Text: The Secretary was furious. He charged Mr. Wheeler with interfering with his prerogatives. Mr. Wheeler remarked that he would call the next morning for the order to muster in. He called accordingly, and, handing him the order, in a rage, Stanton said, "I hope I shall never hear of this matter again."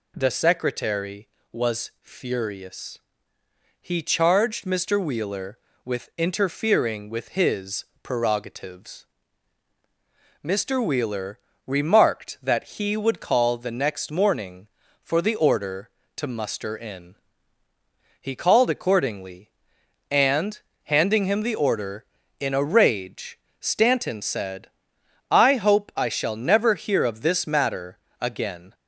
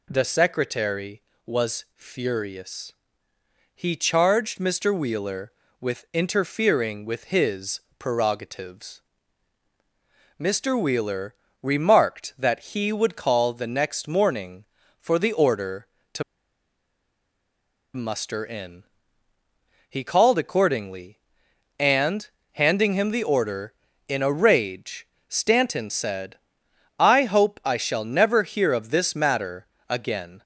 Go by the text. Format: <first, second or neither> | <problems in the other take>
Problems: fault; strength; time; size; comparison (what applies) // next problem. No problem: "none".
first | pauses between "his" and "prerogatives"; slight; at 7.8 s; 0.18 s long; slight in the first // pauses between "Wheeler" and "remarked"; slight; at 11.3 s; 0.26 s long; slight in the first // pauses between "to" and "muster"; strong; at 16.2 s; 1.7 s long // pauses between "matter" and "again"; slight; at 29.6 s; 0.22 s long; slight in the first